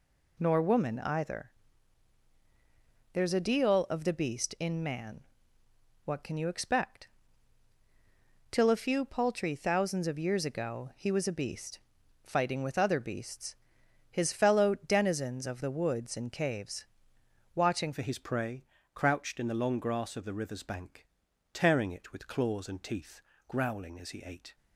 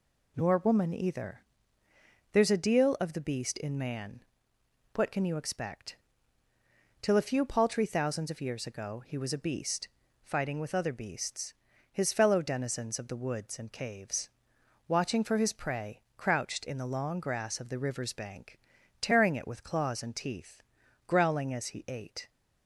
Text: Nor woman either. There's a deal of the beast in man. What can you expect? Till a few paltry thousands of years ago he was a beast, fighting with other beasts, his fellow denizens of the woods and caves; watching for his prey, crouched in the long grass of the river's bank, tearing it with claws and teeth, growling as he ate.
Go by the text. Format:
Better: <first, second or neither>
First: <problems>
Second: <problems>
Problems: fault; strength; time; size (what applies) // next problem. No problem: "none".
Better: second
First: changes voice at "for"; from 17.9 s on; 6.6 s long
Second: none